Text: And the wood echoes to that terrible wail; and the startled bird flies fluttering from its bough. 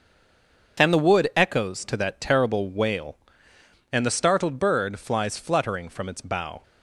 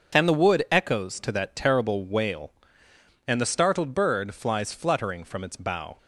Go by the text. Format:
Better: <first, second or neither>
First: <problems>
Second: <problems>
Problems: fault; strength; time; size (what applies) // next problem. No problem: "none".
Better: second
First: stays silent before the first word; slight; until 0.7 s; 0.7 s long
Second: none